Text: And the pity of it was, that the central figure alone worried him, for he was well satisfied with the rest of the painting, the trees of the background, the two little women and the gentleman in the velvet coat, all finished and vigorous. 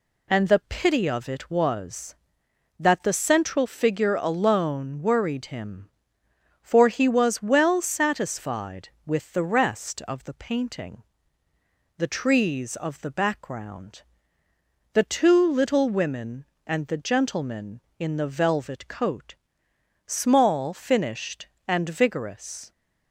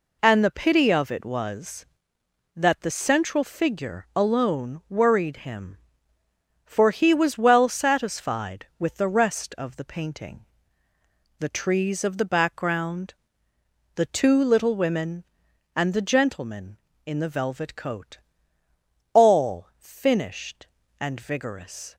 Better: second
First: says "small" for "all"; at 20.0 s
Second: none

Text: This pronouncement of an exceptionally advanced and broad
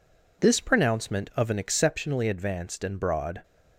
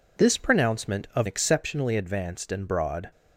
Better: first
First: none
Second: skips "an"; at 1.2 s

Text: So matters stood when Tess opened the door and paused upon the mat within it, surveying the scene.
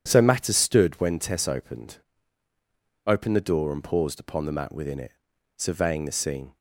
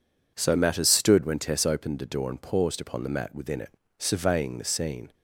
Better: second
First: says "opened" twice; at 3.0 s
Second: none

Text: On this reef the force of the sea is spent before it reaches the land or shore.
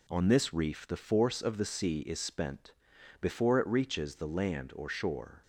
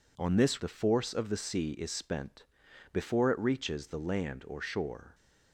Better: first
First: pauses between "spent" and "before"; noticeable; at 2.7 s; 0.48 s long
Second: skips "reef"; at 0.6 s // pauses between "spent" and "before"; noticeable; at 2.4 s; 0.48 s long

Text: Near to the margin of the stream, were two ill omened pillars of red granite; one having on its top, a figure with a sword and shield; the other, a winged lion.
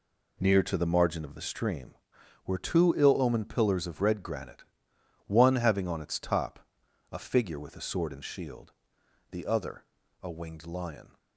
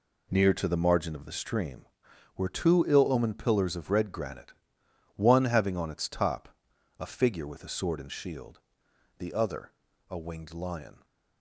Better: neither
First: none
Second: none

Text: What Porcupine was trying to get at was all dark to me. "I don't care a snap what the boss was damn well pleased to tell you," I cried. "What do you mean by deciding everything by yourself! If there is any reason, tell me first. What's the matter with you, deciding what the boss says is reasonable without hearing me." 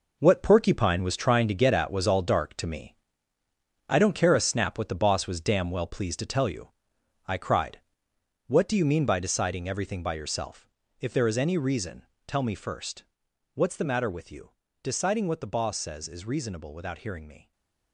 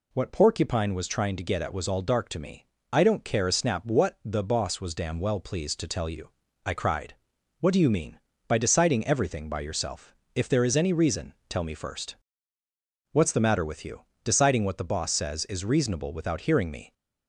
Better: second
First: gets quieter; strong; throughout; 9.5 dB // stays silent after the last word; slight; from 17.4 s on; 0.5 s long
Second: none

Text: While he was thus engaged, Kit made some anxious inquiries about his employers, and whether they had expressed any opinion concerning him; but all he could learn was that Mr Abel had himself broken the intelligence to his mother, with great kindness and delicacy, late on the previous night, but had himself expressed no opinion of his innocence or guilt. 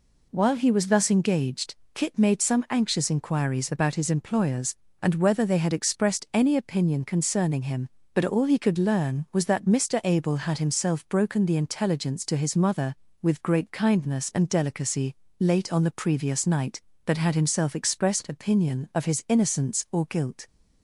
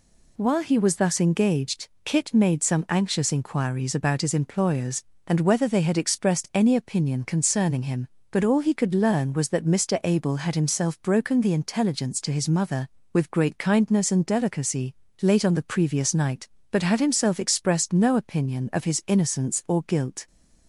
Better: second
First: skips "no"; at 18.2 s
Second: none

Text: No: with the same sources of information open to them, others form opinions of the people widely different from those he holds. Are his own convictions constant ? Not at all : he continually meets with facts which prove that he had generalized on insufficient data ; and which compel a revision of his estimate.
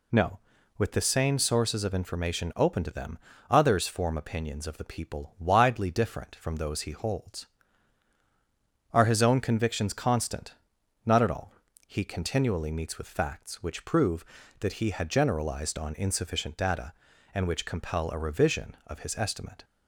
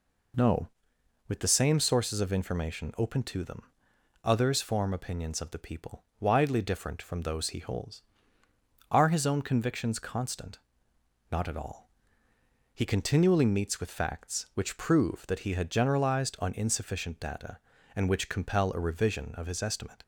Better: neither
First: none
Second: none

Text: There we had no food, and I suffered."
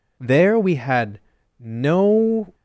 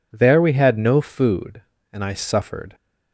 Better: second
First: pauses between "had" and "no"; at 1.1 s; 0.40 s long // stops before "food and I suffered"; at 2.5 s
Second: none

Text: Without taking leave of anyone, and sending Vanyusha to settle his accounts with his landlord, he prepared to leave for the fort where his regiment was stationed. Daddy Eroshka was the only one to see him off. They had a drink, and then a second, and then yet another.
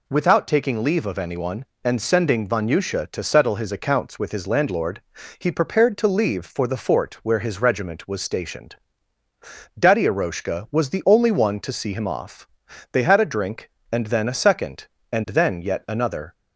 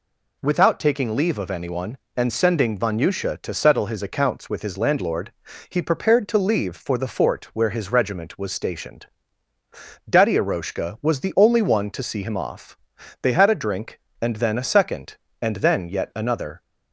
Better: neither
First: none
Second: none

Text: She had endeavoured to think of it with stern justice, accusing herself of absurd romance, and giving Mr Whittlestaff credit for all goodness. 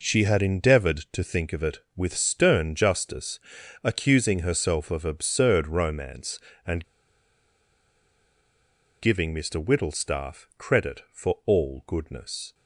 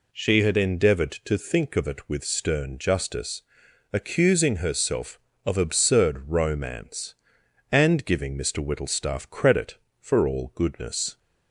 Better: second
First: pauses between "and" and "giving"; strong; at 6.8 s; 2.1 s long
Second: none

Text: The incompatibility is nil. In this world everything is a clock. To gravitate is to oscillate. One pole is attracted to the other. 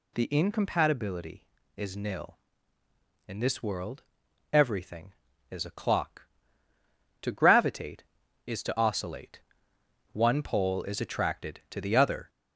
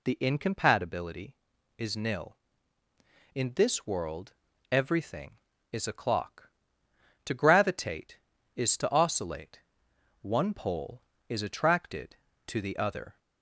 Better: second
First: gets louder; slight; throughout; 2 dB // pauses between "world" and "everything"; noticeable; at 4.0 s; 0.48 s long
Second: pauses between "world" and "everything"; at 4.3 s; 0.38 s long

